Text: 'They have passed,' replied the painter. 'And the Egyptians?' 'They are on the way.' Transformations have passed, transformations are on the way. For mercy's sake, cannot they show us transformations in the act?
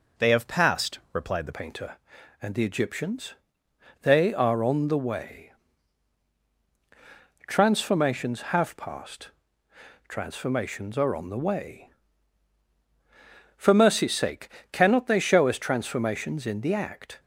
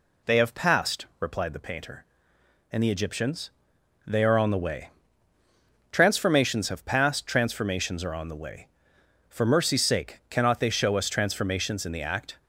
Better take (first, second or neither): second